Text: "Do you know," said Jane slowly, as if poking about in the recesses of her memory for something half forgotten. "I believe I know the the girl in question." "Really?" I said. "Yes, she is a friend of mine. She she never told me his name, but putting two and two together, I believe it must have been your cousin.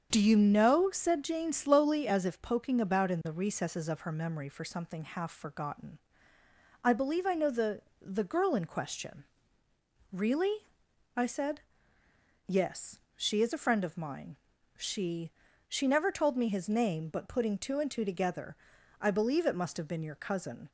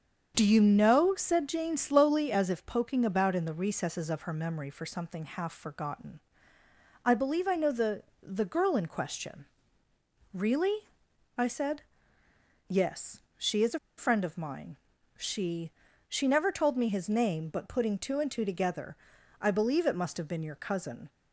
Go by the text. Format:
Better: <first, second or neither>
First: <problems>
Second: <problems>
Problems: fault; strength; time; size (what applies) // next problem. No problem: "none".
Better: first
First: starts louder than the rest; strong; until 1.1 s; 7.5 dB // pauses between "the" and "the"; slight; at 7.8 s; 0.18 s long // pauses between "She" and "she"; slight; at 15.3 s; 0.36 s long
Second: starts louder than the rest; strong; until 1.3 s; 7.5 dB // pauses between "the" and "the"; slight; at 8.0 s; 0.18 s long // pauses between "a" and "friend"; slight; at 13.7 s; 0.19 s long // pauses between "She" and "she"; slight; at 15.7 s; 0.36 s long